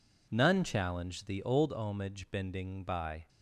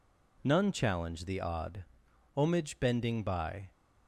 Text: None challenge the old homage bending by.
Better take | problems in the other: first | says "odd" for "old"; at 1.4 s

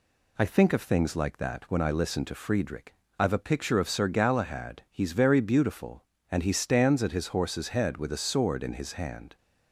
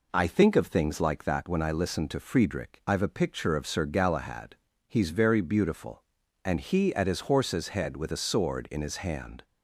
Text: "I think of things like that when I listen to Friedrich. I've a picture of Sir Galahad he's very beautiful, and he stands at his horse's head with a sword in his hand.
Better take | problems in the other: first | pauses between "Galahad" and "he's"; slight; at 4.5 s; 0.32 s long // skips "stands"; at 6.9 s

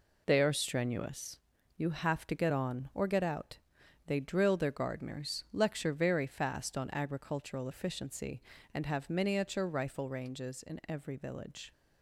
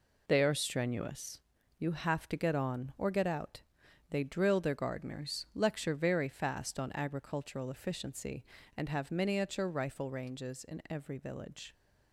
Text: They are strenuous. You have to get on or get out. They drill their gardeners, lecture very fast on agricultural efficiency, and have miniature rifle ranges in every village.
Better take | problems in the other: neither | none

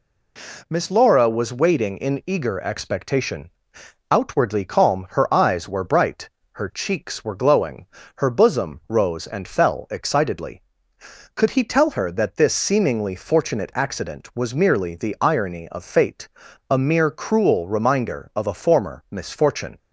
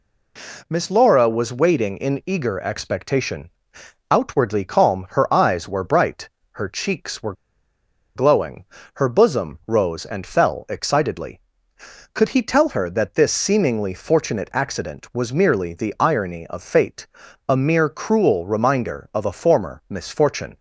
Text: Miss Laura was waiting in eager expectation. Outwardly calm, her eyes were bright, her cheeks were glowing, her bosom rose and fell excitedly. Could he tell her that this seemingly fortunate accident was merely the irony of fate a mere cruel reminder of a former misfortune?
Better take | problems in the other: first | pauses between "were" and "glowing"; noticeable; at 7.3 s; 0.83 s long // pauses between "fate" and "a"; at 17.0 s; 0.42 s long; also in the first

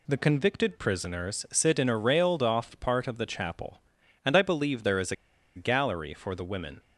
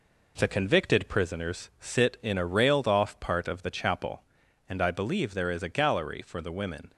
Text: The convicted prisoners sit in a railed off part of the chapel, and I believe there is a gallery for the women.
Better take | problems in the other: second | pauses between "a" and "gallery"; at 5.1 s; 0.41 s long

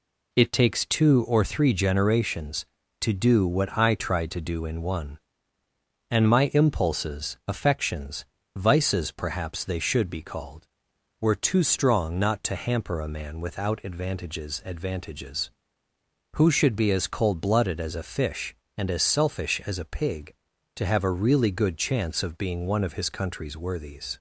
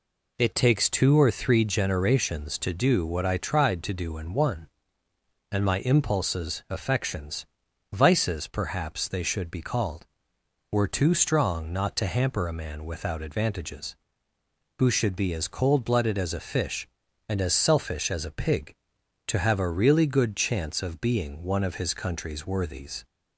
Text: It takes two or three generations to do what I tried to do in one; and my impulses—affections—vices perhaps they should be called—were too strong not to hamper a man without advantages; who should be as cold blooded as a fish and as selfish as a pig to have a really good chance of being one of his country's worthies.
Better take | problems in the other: second | says "advantages" twice; at 14.6 s

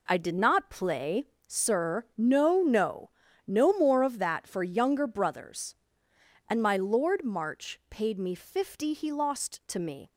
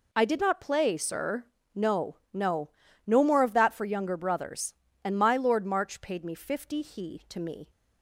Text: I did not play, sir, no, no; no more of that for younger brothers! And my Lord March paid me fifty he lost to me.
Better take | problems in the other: first | skips "lost"; at 7.2 s

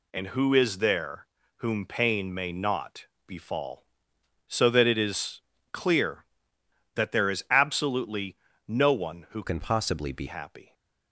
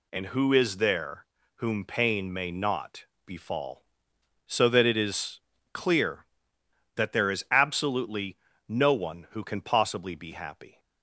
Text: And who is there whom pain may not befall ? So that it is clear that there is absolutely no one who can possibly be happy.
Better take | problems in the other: second | pauses between "there" and "whom"; slight; at 1.2 s; 0.30 s long; slight in the second // pauses between "not" and "befall"; slight; at 3.0 s; 0.20 s long; slight in the second // pauses between "is" and "clear"; slight; at 5.4 s; 0.32 s long; slight in the second // pauses between "absolutely" and "no"; slight; at 8.3 s; 0.30 s long; slight in the second // changes voice from "can" to "be"; from 9.4 to 10.2 s; 0.8 s long

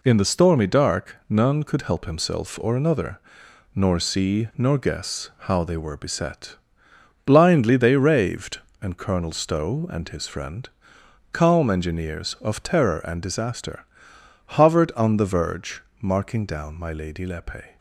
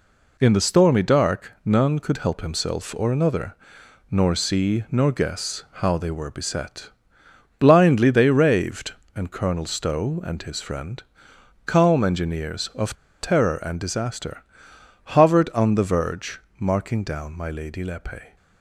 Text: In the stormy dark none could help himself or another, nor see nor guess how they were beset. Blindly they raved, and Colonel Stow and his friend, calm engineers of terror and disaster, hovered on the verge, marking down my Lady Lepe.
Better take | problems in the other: first | pauses between "guess" and "how"; slight; at 5.6 s; 0.18 s long; slight in the first // pauses between "of" and "terror"; slight; at 12.9 s; 0.24 s long

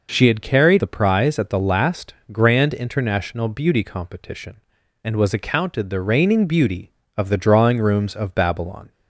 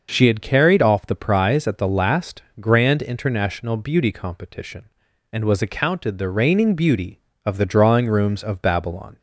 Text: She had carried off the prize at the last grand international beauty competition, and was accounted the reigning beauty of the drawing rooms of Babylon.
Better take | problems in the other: second | skips "off"; at 0.7 s // pauses between "last" and "grand"; slight; at 2.1 s; 0.18 s long; slight in the second

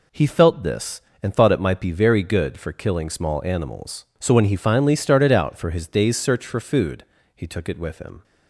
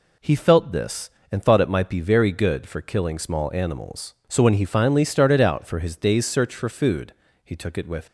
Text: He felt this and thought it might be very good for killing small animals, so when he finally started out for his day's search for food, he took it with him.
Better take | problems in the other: first | stops before "him"; at 8.0 s

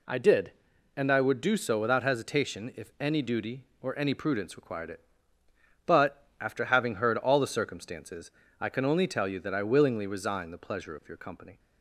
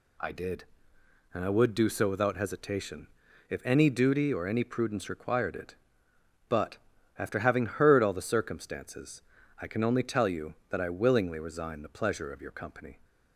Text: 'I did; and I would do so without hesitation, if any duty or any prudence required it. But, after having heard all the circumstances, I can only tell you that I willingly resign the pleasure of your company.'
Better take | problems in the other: neither | none

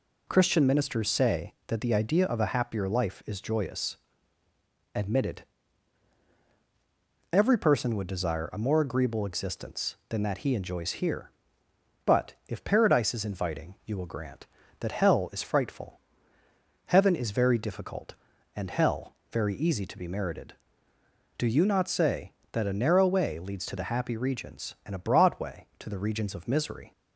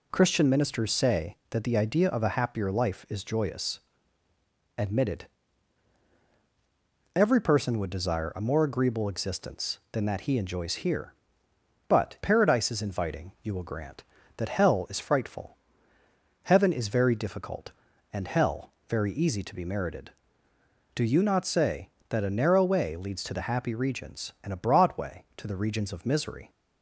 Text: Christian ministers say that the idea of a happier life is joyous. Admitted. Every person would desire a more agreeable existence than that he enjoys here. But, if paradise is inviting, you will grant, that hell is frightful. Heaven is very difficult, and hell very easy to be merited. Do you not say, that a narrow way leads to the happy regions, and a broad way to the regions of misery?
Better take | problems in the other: first | skips "if"; at 12.1 s // pauses between "hell" and "very"; slight; at 18.7 s; 0.18 s long; slight in the first

